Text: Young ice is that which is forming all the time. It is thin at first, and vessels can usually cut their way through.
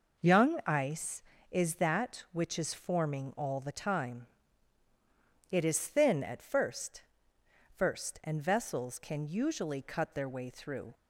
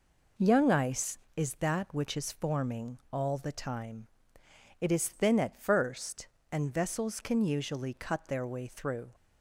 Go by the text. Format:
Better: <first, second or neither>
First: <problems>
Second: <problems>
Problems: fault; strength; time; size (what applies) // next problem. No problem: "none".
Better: second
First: says "first" twice; at 7.7 s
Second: none